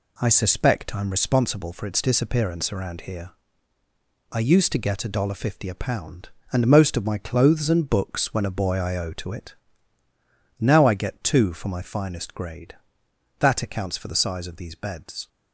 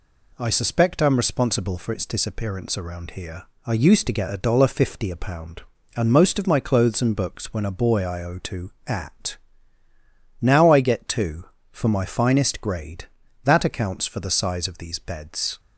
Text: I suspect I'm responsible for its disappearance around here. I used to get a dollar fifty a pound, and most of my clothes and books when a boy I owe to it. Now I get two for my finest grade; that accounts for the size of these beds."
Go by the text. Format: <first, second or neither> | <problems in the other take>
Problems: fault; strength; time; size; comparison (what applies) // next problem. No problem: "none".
first | says "at" for "it"; at 8.8 s